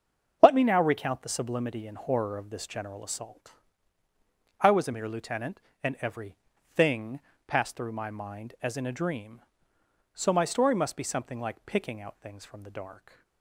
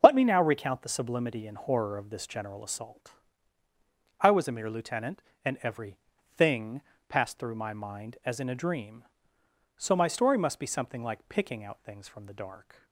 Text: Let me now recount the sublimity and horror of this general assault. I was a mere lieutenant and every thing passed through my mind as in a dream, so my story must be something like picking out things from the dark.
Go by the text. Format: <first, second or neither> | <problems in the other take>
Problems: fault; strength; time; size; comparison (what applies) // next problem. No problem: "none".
neither | starts louder than the rest; the same in both // pauses between "every" and "thing"; the same in both // pauses between "thing" and "passed"; slight; the same in both